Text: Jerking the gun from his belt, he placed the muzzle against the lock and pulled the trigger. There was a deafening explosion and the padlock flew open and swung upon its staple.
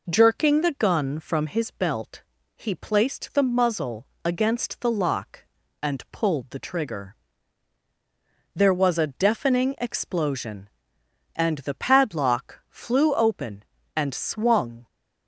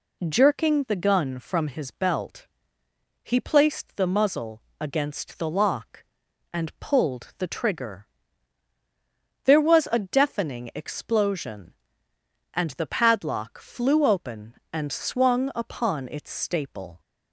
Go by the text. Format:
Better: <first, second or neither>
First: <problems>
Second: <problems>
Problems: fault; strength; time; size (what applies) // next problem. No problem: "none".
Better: second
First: pauses between "muzzle" and "against"; slight; at 4.0 s; 0.20 s long // stops before "upon its staple"; at 14.8 s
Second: pauses between "muzzle" and "against"; slight; at 4.6 s; 0.18 s long